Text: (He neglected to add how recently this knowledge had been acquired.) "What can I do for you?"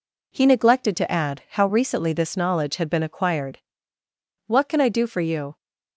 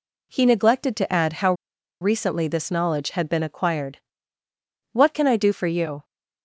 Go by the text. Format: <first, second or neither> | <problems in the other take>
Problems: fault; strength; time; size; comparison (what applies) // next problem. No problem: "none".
first | pauses between "how" and "recently"; noticeable; at 1.5 s; 0.48 s long